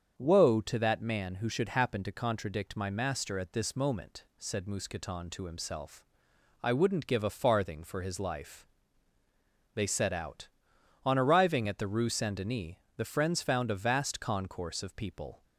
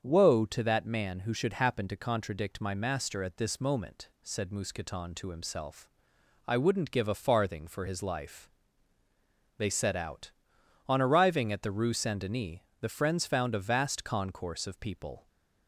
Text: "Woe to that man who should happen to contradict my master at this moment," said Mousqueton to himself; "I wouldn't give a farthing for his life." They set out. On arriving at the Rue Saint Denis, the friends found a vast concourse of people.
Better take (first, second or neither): neither